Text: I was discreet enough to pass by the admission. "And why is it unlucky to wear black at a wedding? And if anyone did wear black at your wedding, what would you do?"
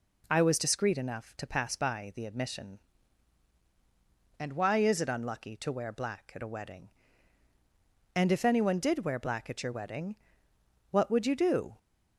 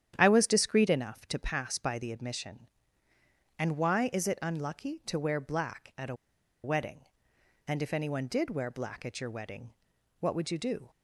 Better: first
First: none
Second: starts louder than the rest; strong; until 1.1 s; 9.5 dB // pauses between "a" and "wedding"; noticeable; at 6.1 s; 0.49 s long

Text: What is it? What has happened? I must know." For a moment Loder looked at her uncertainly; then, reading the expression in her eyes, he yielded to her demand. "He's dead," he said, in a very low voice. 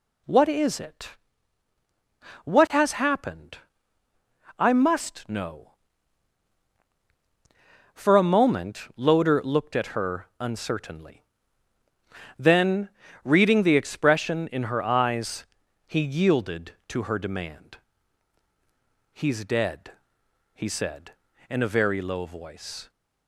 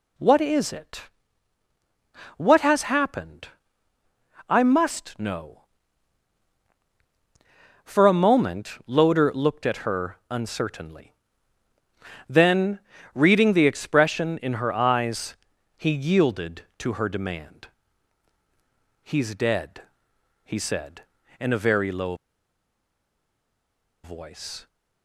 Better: first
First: none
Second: pauses between "low" and "voice"; strong; at 22.1 s; 1.8 s long

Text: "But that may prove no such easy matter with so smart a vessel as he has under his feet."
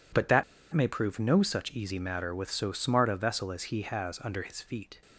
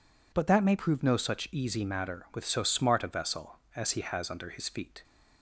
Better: second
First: pauses between "that" and "may"; slight; at 0.4 s; 0.29 s long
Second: none

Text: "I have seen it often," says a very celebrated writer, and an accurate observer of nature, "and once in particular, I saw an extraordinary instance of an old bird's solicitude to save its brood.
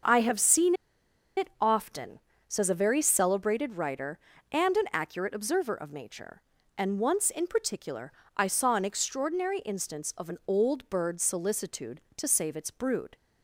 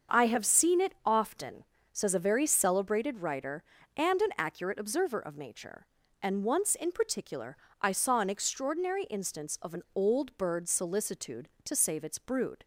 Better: second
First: starts louder than the rest; until 1.7 s; 6.5 dB // pauses between "seen" and "it"; noticeable; at 0.7 s; 0.63 s long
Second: starts louder than the rest; until 1.2 s; 6.5 dB

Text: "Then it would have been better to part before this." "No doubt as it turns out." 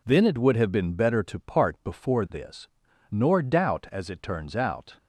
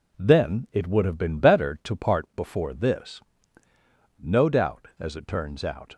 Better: second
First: says "Nor" for "No"; at 3.1 s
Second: none

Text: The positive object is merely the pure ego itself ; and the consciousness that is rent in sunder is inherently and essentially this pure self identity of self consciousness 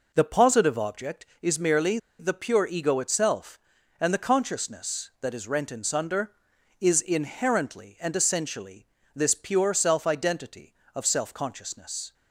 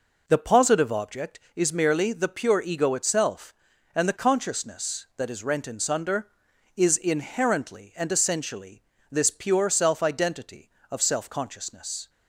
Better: second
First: pauses between "merely" and "the"; slight; at 1.9 s; 0.20 s long // pauses between "essentially" and "this"; slight; at 8.8 s; 0.26 s long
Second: pauses between "essentially" and "this"; slight; at 8.8 s; 0.26 s long

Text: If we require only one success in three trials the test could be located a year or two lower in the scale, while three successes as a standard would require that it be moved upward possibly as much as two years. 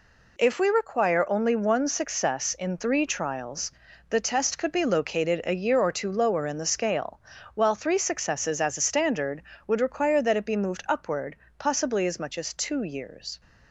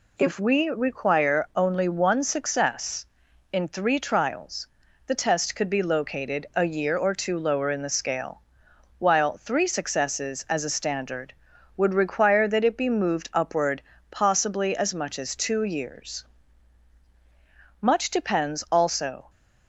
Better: first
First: pauses between "trials" and "the"; at 3.7 s; 0.38 s long // pauses between "upward" and "possibly"; slight; at 11.3 s; 0.22 s long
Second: pauses between "trials" and "the"; at 4.6 s; 0.40 s long // pauses between "upward" and "possibly"; slight; at 13.7 s; 0.30 s long // goes on to say "Much depends also"; from 17.7 s on; 1.5 s long

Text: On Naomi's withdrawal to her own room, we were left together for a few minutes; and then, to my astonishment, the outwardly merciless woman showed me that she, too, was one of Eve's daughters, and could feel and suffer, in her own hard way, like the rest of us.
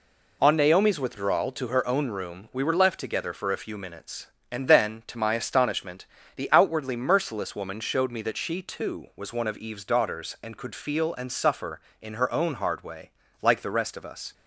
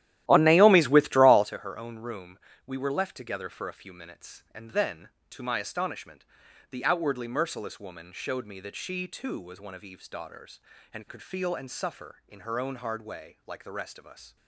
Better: first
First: none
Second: starts louder than the rest; strong; until 1.5 s; 13.5 dB

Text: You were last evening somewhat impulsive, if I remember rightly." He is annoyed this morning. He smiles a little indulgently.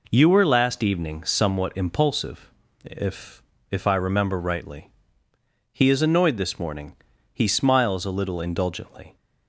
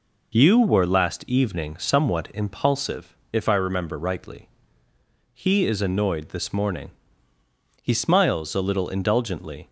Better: second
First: says "if" twice; at 3.7 s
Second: none

